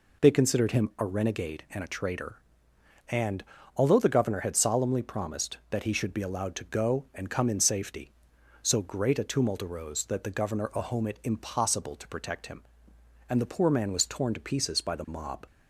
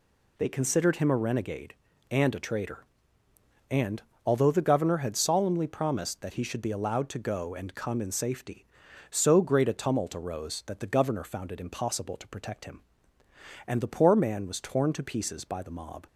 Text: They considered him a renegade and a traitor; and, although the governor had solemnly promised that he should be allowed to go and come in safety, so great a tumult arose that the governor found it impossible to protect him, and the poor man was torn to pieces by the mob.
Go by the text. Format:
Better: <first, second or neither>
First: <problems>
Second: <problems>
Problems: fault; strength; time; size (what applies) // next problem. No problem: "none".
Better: second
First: says "ahome" for "found"; at 10.7 s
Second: none